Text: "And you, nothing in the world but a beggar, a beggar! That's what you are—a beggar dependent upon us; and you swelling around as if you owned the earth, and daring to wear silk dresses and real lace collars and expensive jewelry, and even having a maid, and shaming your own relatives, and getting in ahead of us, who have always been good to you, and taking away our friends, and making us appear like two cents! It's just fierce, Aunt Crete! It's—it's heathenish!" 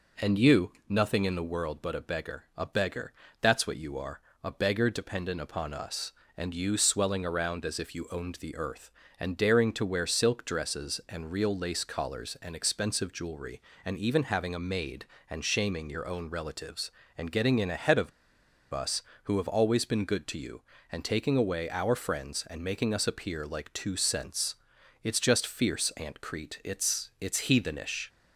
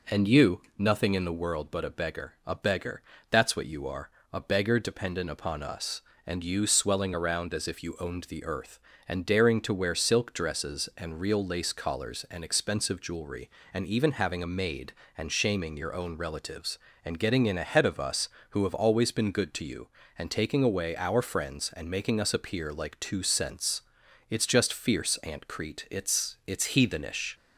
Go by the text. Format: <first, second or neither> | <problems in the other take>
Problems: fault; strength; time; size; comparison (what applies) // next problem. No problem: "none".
second | pauses between "of" and "us"; noticeable; at 18.1 s; 0.62 s long